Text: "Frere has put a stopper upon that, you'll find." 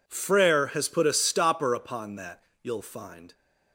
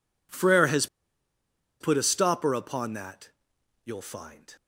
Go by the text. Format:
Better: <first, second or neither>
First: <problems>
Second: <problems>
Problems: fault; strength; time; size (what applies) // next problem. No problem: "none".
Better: first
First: none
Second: pauses between "has" and "put"; noticeable; at 0.8 s; 0.94 s long